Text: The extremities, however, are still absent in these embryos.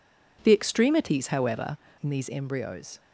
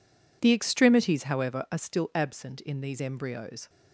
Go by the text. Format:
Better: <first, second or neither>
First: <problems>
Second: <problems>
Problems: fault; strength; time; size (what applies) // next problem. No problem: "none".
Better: second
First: skips "are still absent"; at 1.8 s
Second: none